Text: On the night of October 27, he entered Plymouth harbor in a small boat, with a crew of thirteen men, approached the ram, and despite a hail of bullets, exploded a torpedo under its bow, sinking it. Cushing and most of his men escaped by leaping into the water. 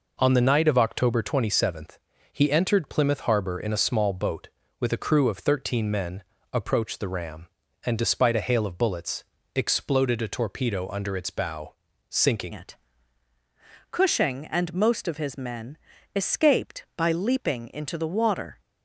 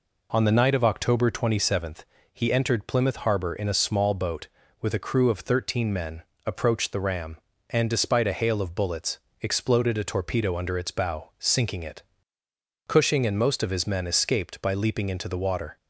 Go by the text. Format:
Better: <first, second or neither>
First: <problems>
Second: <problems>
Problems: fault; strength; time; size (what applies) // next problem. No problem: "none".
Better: second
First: changes voice at "it"; from 12.5 s on; 6.1 s long // pauses between "men" and "escaped"; at 15.7 s; 0.38 s long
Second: none